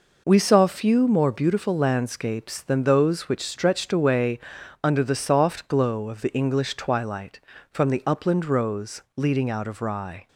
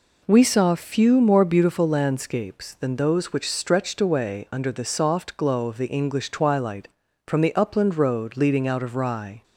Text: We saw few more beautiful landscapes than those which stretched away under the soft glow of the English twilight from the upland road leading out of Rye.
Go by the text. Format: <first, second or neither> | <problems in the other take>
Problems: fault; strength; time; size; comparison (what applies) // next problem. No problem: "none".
second | pauses between "away" and "under"; noticeable; at 4.3 s; 0.46 s long // says "rose" for "road"; at 8.4 s